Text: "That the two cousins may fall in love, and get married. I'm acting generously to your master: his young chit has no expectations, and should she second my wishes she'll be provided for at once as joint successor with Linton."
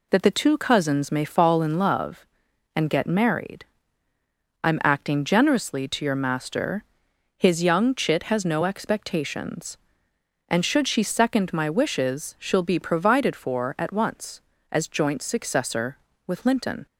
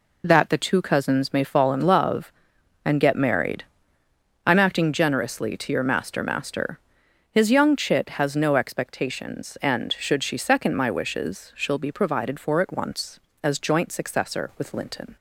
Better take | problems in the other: first | says "master" twice; at 6.2 s

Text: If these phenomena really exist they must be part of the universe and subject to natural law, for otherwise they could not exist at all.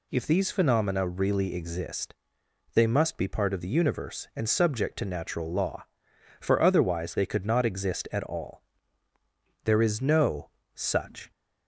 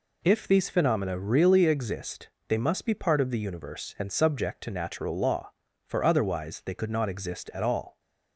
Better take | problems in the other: second | pauses between "exist" and "they"; noticeable; at 2.1 s; 0.60 s long; slight in the second // goes on to say "There is no such"; from 9.6 s on; 1.6 s long

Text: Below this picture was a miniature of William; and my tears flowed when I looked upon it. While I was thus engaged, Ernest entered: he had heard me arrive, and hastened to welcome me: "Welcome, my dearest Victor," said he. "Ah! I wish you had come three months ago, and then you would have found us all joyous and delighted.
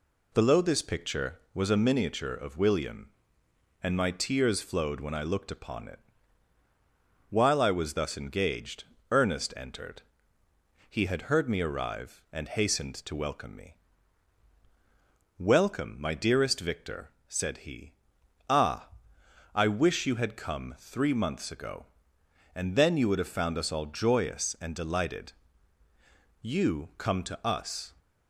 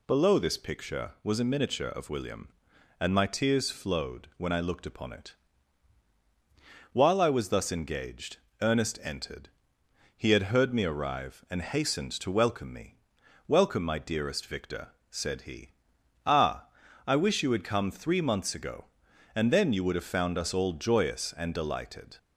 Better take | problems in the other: second | goes on to say "You come to us"; from 26.4 s on; 1.5 s long

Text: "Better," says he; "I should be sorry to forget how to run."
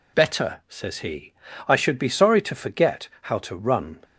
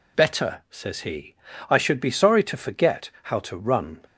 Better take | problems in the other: neither | none

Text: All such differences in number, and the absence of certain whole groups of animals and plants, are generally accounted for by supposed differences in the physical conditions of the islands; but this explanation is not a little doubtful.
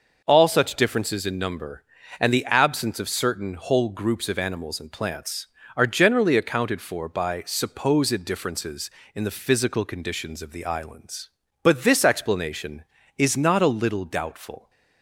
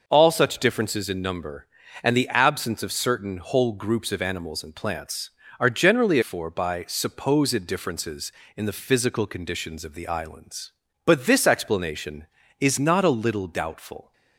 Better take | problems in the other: first | skips "accounted"; at 6.2 s

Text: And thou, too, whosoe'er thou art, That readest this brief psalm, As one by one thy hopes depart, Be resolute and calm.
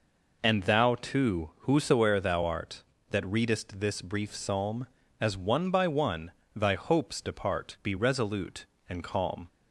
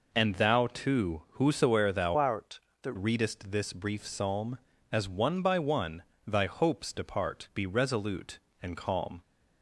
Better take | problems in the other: first | changes voice from "art" to "That"; from 2.1 to 2.9 s; 0.8 s long // pauses between "one" and "thy"; slight; at 6.0 s; 0.24 s long; slight in the first

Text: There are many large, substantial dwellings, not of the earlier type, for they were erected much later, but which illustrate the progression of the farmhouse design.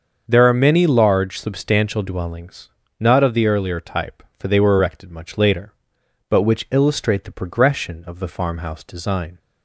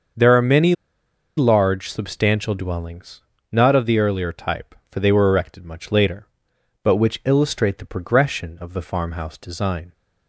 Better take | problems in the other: first | starts louder than the rest; until 1.8 s; 6.5 dB; also in the first // pauses between "many" and "large"; noticeable; at 0.7 s; 0.63 s long

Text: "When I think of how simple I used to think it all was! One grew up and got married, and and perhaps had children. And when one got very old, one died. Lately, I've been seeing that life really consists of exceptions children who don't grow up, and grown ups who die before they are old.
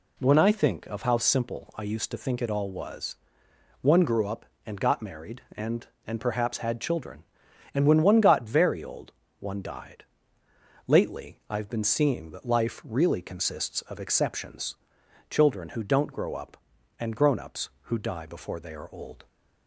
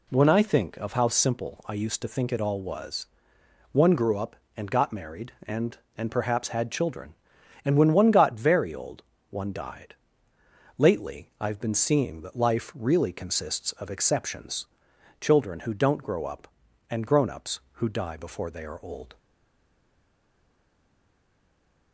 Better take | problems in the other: first | pauses between "exceptions" and "children"; noticeable; at 14.6 s; 0.56 s long; noticeable in the first // stays silent after the last word; strong; from 19.1 s on; 2.8 s long

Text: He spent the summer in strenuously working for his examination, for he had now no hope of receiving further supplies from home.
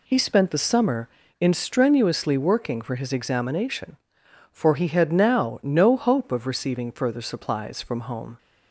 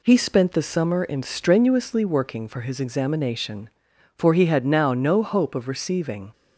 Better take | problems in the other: first | stops before "further supplies from home"; at 6.3 s

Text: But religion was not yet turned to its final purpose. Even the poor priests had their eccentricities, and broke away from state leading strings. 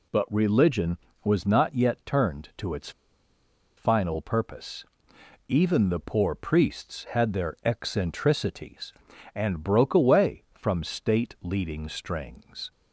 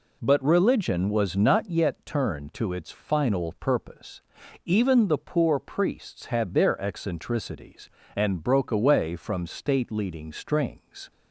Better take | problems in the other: second | pauses between "its" and "final"; noticeable; at 2.9 s; 0.86 s long

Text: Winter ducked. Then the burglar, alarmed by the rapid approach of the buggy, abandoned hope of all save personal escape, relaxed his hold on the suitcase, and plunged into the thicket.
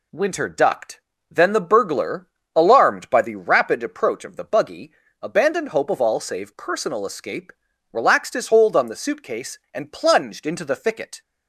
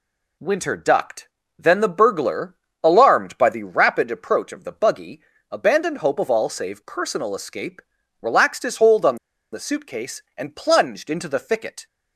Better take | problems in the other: first | pauses between "on" and "the"; at 9.1 s; 0.36 s long

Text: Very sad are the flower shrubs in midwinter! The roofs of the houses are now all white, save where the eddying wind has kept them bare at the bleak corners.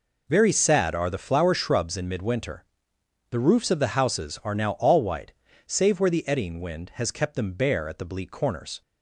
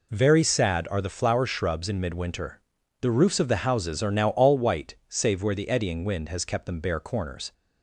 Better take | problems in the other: first | skips "at the bleak"; at 6.9 s

